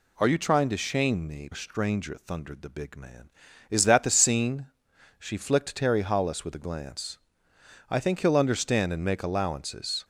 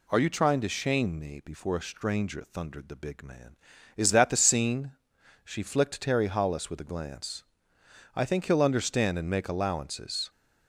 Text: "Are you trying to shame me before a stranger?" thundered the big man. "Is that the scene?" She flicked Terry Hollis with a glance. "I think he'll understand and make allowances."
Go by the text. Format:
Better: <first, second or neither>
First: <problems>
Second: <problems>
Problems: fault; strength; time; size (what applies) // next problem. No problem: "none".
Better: second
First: skips "before"; at 1.5 s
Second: none